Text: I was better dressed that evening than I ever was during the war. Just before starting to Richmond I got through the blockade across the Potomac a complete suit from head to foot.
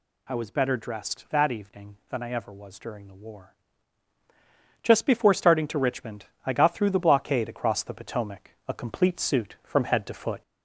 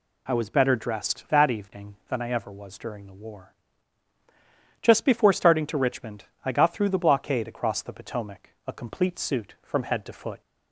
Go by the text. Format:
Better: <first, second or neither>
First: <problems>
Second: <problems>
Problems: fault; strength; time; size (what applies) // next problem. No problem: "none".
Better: second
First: gets louder; slight; throughout; 2.5 dB // pauses between "Richmond" and "I"; slight; at 6.2 s; 0.20 s long // pauses between "Potomac" and "a"; slight; at 8.4 s; 0.18 s long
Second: pauses between "Richmond" and "I"; slight; at 6.2 s; 0.20 s long // pauses between "Potomac" and "a"; slight; at 8.4 s; 0.18 s long